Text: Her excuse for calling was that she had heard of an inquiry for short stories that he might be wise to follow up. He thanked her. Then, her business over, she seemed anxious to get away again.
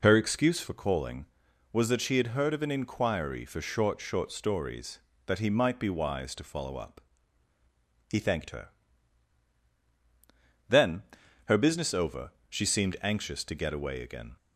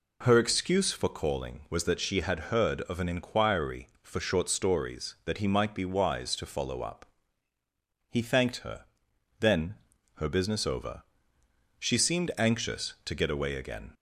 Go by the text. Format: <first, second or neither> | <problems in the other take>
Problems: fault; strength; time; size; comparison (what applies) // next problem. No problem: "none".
second | says "short" twice; at 4.0 s